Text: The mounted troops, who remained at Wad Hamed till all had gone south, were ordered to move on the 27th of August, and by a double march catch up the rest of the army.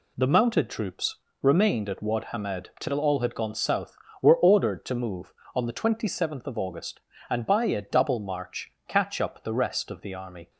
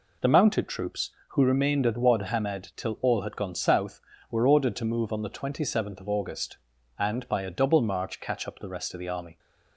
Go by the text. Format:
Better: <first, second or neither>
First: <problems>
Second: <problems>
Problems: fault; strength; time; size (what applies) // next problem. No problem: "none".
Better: second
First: skips "who"; at 1.2 s // pauses between "march" and "catch"; slight; at 8.6 s; 0.16 s long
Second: none